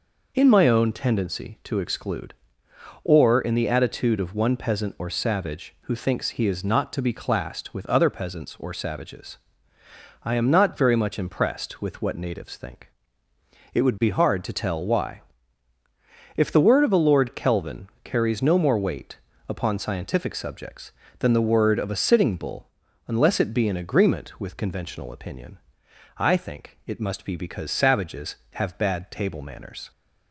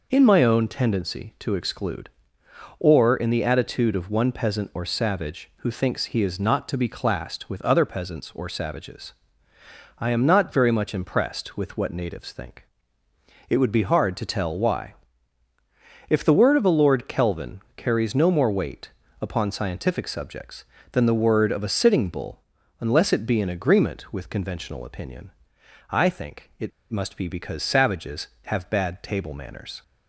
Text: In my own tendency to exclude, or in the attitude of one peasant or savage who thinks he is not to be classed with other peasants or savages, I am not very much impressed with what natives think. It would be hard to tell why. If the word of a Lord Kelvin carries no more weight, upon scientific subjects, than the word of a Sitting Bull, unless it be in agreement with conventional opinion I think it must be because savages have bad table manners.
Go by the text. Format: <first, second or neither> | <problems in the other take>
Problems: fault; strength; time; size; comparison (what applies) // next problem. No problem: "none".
first | pauses between "Kelvin" and "carries"; slight; at 17.5 s; 0.16 s long; slight in the first // pauses between "opinion" and "I"; noticeable; at 25.3 s; 0.58 s long; noticeable in the first // pauses between "it" and "must"; slight; at 26.7 s; 0.19 s long